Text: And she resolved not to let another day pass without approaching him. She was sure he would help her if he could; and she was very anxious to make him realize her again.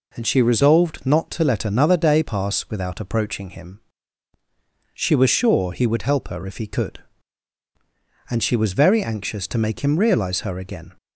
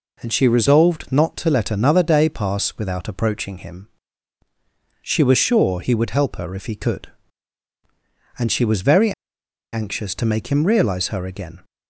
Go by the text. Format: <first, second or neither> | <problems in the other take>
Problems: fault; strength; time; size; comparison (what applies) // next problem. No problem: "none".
first | pauses between "very" and "anxious"; noticeable; at 9.1 s; 0.60 s long